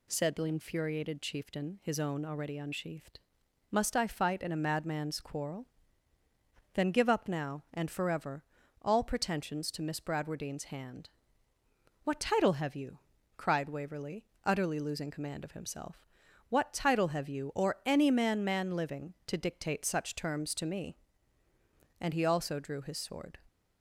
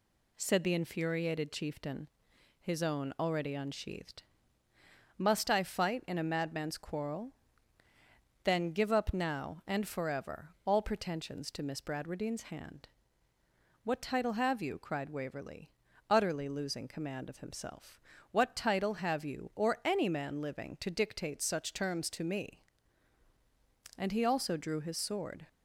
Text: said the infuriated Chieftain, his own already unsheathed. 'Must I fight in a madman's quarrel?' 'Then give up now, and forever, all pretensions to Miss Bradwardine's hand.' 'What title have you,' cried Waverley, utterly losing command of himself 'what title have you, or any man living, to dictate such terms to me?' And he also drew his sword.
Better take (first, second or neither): second